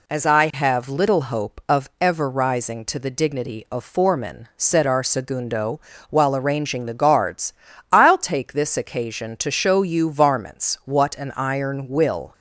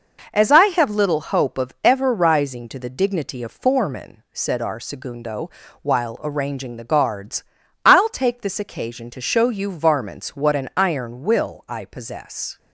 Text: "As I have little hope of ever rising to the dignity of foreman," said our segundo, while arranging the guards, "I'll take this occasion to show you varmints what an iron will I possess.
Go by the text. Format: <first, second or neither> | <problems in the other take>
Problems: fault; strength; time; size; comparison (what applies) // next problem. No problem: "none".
second | stops before "I possess"; at 12.3 s